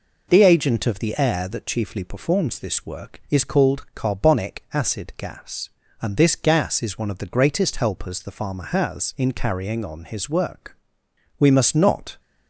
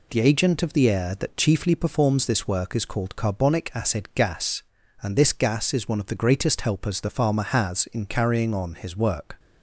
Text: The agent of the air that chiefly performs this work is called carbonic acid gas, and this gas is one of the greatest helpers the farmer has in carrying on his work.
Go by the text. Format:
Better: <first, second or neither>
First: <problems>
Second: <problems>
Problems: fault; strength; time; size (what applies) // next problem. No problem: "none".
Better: second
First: goes on to say "We must not"; noticeable; from 11.3 s on; 0.80 s long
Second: none